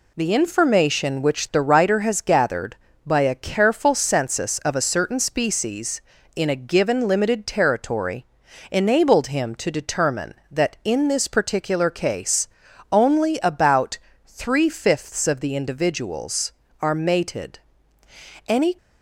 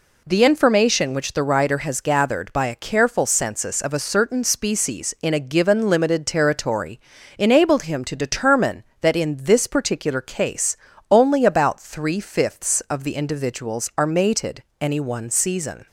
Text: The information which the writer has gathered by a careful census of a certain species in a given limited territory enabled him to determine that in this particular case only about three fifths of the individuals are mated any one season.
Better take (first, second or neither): second